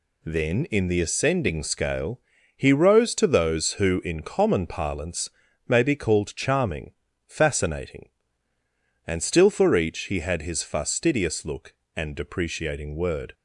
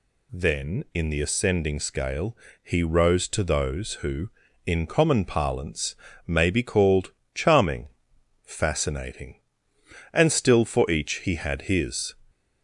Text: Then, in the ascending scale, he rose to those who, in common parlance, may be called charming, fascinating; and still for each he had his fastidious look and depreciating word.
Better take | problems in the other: first | pauses between "called" and "charming"; slight; at 7.1 s; 0.22 s long // stops before "fastidious look and depreciating word"; at 12.2 s

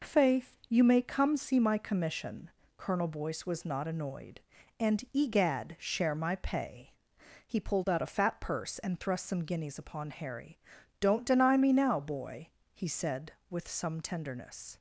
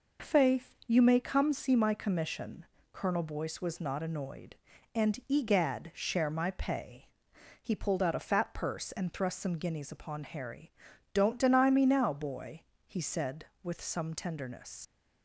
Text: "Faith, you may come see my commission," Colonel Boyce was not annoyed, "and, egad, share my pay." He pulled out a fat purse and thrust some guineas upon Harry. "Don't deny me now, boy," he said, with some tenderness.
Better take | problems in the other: first | leaves "tenderness" unfinished; at 14.8 s; 50 ms

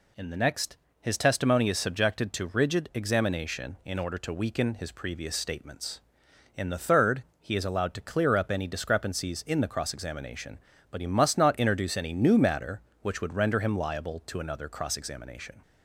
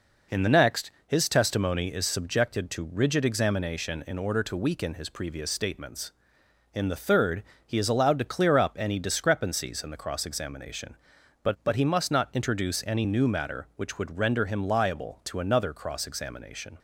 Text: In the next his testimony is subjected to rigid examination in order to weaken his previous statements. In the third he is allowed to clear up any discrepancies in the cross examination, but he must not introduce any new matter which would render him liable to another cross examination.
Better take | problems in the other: first | pauses between "next" and "his"; slight; at 0.9 s; 0.16 s long; slight in the first // pauses between "third" and "he"; slight; at 7.4 s; 0.22 s long; slight in the first // says "but" twice; at 11.6 s

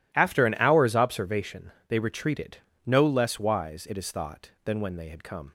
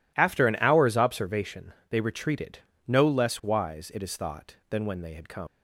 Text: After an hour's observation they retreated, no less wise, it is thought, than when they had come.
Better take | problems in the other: first | pauses between "observation" and "they"; slight; at 1.7 s; 0.16 s long; slight in the first // leaves "come" unfinished; at 5.4 s; 95 ms

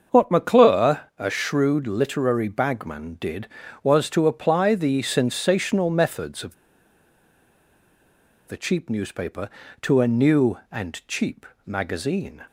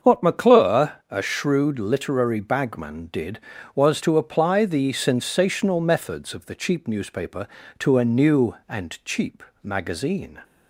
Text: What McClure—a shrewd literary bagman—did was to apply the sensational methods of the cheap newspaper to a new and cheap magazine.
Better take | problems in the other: second | starts louder than the rest; until 1.2 s; 6.5 dB; also in the second // pauses between "of" and "the"; strong; at 6.5 s; 1.9 s long // pauses between "cheap" and "magazine"; slight; at 11.4 s; 0.18 s long; slight in the second

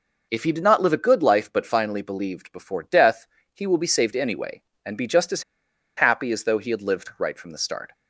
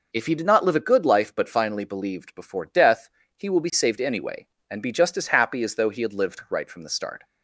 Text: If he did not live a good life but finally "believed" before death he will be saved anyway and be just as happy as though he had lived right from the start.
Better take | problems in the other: second | pauses between "death" and "he"; slight; at 3.2 s; 0.30 s long; slight in the second // pauses between "as" and "happy"; noticeable; at 5.4 s; 0.54 s long

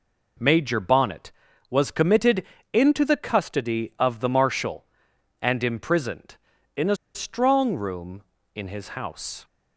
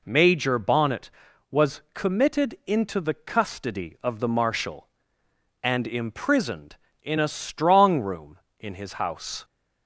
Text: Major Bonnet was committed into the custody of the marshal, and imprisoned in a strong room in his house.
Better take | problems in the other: second | pauses between "committed" and "into"; slight; at 2.4 s; 0.28 s long // pauses between "a" and "strong"; slight; at 6.9 s; 0.19 s long

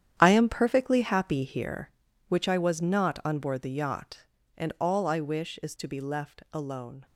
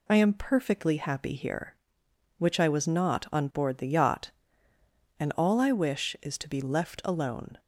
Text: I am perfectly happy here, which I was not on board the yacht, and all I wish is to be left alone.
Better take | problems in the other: second | gets quieter; strong; throughout; 11.5 dB

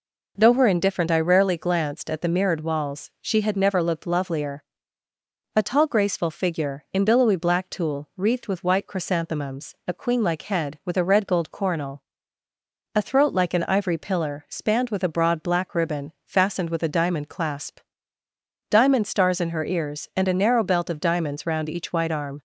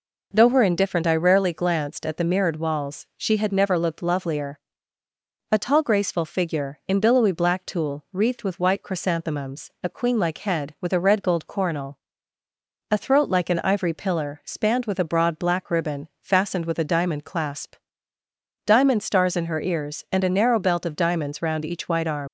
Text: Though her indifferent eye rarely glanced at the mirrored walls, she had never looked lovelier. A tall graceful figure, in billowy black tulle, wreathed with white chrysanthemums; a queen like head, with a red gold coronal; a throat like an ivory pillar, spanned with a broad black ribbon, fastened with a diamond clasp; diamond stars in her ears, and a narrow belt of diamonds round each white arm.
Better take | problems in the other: first | leaves "arm" unfinished; at 22.2 s; 90 ms

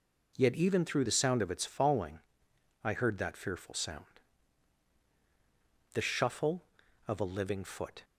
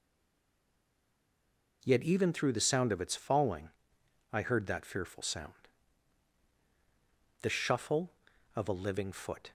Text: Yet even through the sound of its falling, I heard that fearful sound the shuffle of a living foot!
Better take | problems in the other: first | stays silent before the first word; noticeable; until 1.8 s; 1.8 s long // pauses between "sound" and "the"; strong; at 5.5 s; 1.8 s long; strong in the first

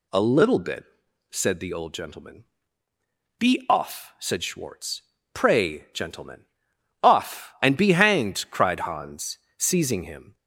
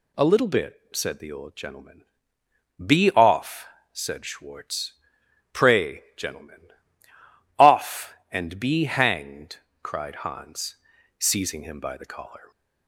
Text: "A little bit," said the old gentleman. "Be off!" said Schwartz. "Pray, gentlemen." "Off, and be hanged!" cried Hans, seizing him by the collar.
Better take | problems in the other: second | stops before "by the collar"; at 10.3 s

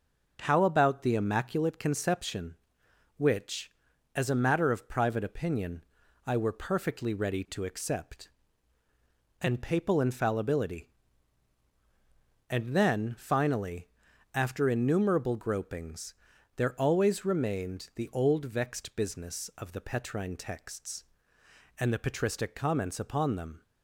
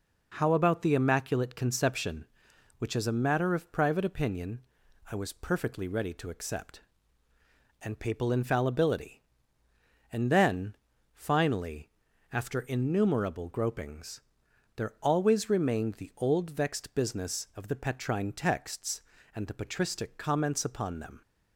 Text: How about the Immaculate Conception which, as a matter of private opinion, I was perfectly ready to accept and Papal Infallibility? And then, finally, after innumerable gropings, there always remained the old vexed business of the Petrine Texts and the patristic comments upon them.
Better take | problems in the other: second | starts louder than the rest; until 1.4 s; 6 dB // says "were" for "was"; at 6.3 s

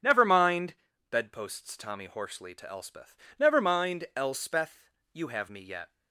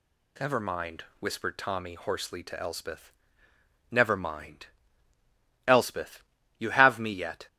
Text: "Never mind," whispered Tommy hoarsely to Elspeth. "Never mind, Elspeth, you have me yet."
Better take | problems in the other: second | starts louder than the rest; strong; until 1.3 s; 8.5 dB // says "bedposts" for "whispered"; at 1.0 s

